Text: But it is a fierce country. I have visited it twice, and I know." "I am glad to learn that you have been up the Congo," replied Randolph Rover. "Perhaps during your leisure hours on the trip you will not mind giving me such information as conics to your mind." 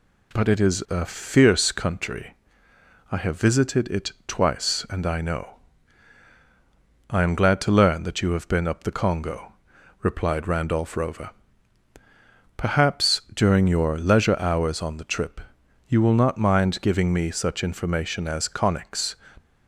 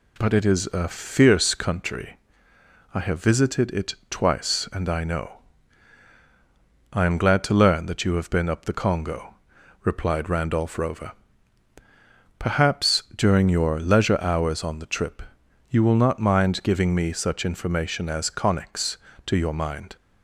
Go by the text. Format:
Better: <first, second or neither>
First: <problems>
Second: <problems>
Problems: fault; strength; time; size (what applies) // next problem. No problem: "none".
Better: second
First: pauses between "trip" and "you"; noticeable; at 15.4 s; 0.46 s long // stops before "to your mind"; at 19.3 s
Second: pauses between "trip" and "you"; noticeable; at 15.2 s; 0.46 s long